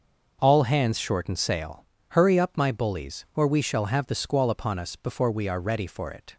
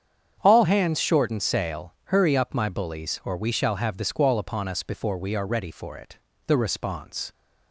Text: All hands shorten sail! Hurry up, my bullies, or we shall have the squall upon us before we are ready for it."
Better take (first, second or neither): first